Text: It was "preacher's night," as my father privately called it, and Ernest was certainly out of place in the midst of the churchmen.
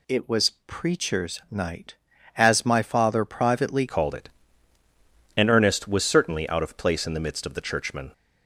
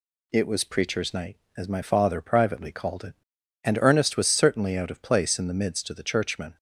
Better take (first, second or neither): second